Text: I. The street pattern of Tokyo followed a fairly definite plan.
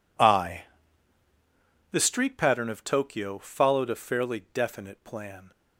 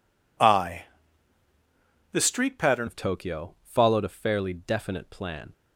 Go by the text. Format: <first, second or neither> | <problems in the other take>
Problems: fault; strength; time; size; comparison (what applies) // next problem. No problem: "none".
first | changes voice at "of"; from 2.8 s on; 2.7 s long